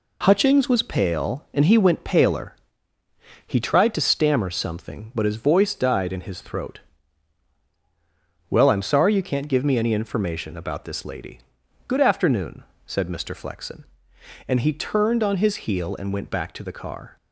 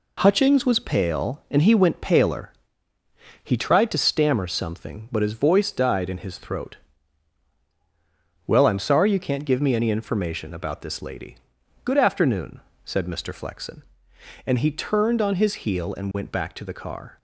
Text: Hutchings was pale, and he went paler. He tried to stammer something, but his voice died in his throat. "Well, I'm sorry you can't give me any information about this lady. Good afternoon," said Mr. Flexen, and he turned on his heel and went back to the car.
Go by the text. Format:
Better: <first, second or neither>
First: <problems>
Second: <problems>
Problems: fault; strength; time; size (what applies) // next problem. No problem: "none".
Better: neither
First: none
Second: none